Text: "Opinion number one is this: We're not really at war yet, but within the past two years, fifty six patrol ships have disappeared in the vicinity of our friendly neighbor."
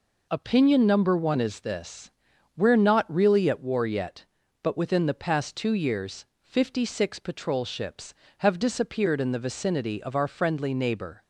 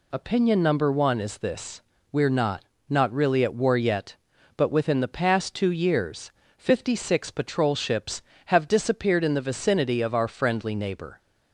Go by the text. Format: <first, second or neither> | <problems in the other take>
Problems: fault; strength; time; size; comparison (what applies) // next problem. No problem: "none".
first | says "not" twice; at 2.8 s